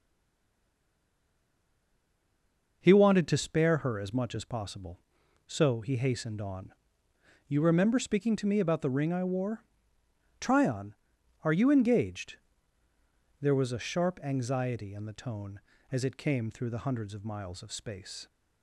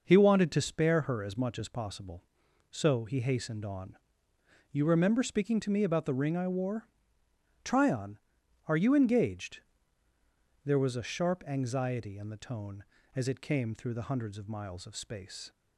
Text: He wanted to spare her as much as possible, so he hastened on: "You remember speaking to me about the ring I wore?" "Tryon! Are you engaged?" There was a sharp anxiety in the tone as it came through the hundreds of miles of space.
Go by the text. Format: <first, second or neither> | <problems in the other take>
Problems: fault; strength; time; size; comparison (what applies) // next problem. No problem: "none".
second | stays silent before the first word; strong; until 2.8 s; 2.8 s long